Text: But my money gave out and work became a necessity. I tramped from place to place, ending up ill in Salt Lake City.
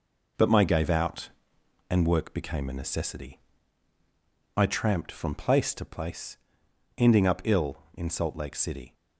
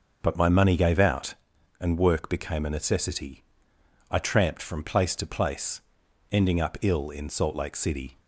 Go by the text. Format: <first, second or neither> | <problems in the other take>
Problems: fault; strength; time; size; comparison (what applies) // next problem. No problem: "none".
second | skips "money"; at 0.6 s